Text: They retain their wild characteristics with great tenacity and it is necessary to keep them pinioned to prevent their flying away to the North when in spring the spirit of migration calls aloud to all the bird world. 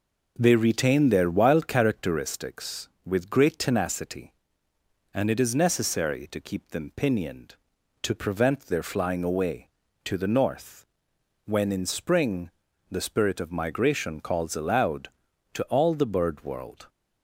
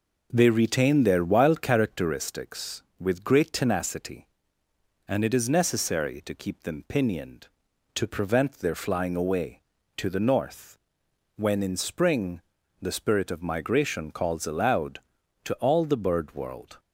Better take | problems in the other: neither | pauses between "North" and "when"; noticeable; the same in both // pauses between "spring" and "the"; the same in both

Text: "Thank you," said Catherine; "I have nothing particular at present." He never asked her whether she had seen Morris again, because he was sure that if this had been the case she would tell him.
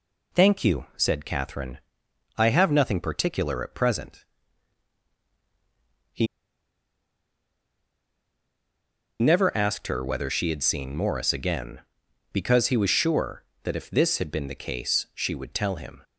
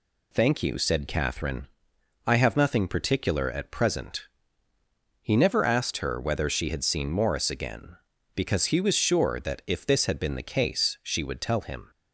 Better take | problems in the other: second | pauses between "He" and "never"; strong; at 6.2 s; 2.9 s long

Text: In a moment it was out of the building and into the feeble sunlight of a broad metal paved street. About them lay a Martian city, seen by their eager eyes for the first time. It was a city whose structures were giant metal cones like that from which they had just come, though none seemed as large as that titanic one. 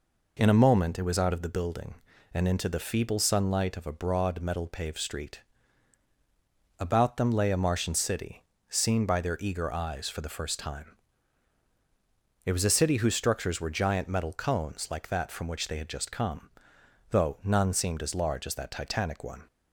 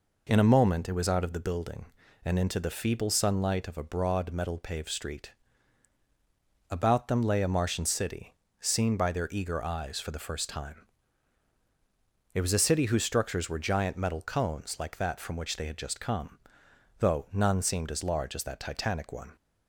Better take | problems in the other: neither | none

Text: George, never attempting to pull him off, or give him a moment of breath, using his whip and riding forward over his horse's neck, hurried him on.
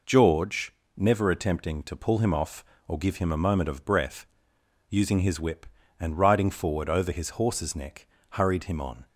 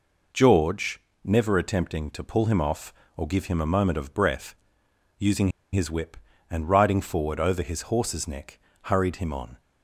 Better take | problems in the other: first | pauses between "using" and "his"; slight; at 5.4 s; 0.25 s long

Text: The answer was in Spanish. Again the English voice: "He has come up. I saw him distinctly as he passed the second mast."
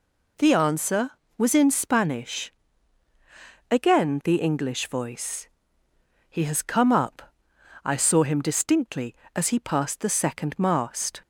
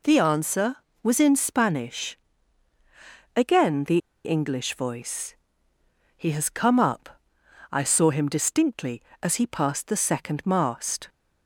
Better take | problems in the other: first | pauses between "the" and "English"; slight; at 3.9 s; 0.26 s long

